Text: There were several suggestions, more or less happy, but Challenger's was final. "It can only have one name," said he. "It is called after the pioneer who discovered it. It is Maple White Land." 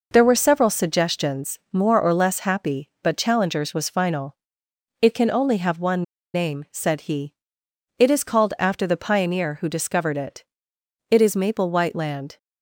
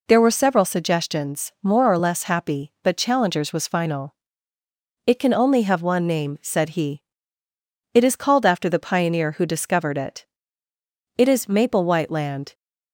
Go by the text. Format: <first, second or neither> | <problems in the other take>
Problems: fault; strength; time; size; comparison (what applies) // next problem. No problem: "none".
second | pauses between "one" and "name"; slight; at 6.0 s; 0.31 s long